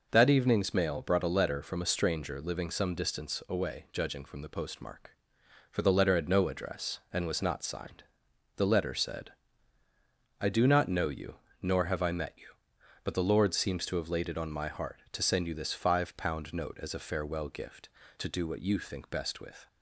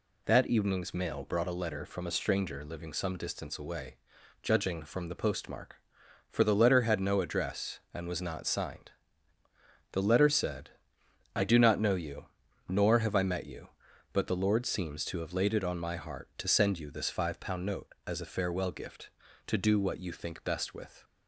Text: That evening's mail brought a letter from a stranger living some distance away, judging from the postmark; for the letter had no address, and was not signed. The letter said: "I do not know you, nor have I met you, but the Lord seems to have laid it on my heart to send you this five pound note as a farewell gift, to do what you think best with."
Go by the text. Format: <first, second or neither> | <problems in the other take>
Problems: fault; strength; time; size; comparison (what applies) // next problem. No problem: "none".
neither | none